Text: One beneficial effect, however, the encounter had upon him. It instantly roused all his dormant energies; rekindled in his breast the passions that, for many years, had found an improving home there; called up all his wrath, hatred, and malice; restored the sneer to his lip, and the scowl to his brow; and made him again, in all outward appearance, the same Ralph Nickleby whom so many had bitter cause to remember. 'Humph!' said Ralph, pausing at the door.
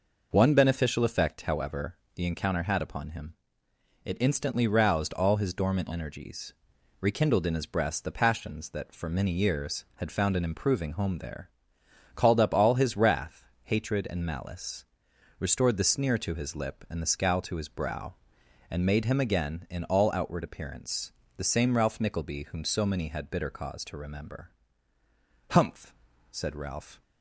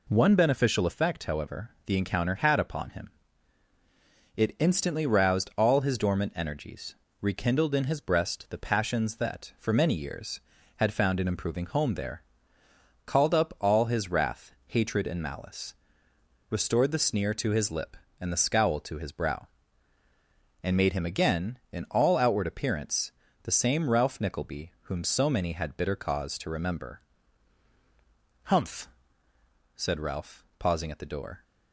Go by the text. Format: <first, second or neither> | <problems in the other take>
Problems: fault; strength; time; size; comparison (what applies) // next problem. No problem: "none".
second | stops before "pausing at the door"; at 27.0 s